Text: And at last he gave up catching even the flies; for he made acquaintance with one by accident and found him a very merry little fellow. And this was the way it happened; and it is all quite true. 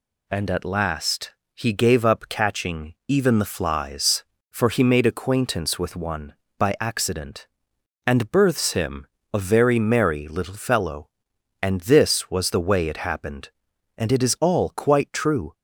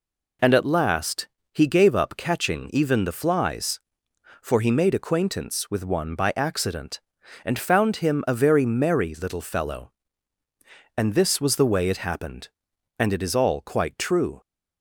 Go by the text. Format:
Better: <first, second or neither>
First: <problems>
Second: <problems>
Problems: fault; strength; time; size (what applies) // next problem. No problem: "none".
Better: second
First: pauses between "last" and "he"; slight; at 1.3 s; 0.24 s long // says "births" for "found"; at 8.3 s // pauses between "him" and "a"; slight; at 9.0 s; 0.26 s long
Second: pauses between "last" and "he"; slight; at 1.2 s; 0.24 s long